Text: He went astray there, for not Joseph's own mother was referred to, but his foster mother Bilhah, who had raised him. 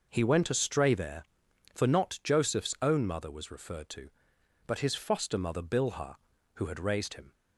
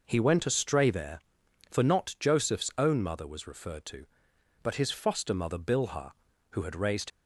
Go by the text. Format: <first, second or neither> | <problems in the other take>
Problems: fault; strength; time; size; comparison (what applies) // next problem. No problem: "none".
first | stops before "him"; at 7.1 s